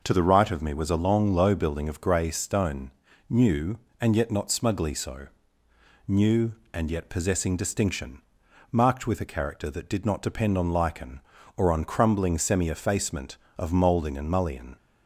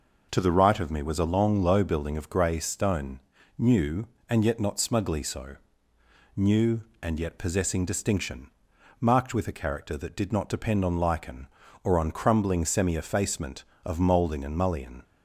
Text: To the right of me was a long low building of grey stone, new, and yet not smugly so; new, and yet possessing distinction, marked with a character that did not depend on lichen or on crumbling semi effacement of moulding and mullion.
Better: neither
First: none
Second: none

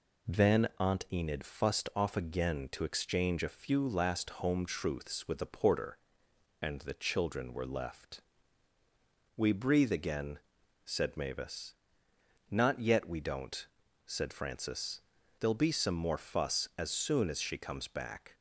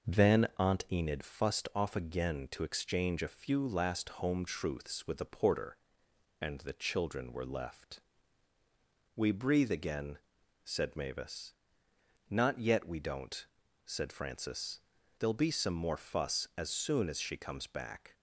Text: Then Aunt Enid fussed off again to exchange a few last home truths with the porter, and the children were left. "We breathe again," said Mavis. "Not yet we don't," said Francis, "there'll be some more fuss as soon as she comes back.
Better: first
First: none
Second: starts louder than the rest; noticeable; until 1.3 s; 5.5 dB

